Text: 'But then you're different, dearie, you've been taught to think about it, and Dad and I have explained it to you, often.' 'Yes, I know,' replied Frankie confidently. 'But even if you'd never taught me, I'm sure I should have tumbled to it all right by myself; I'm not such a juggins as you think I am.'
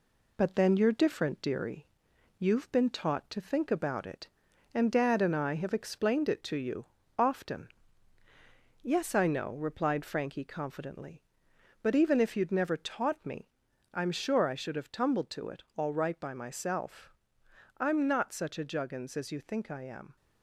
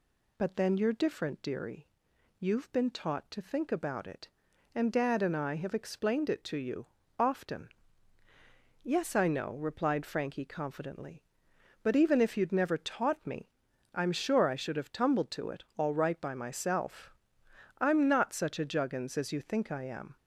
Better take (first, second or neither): second